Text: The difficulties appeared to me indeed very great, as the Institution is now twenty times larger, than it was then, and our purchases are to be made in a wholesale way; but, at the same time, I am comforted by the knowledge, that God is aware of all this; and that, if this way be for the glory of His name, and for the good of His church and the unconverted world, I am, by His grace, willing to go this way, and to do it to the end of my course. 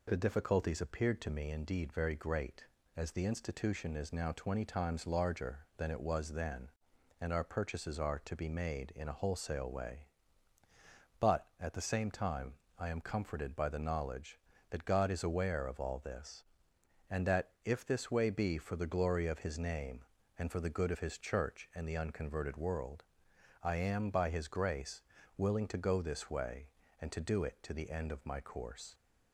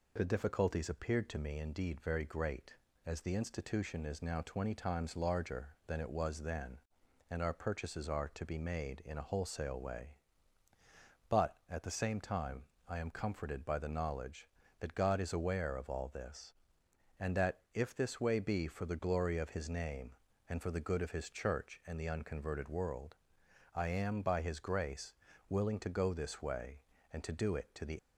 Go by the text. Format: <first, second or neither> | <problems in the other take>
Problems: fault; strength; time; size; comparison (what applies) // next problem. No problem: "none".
first | stops before "end of my course"; at 27.9 s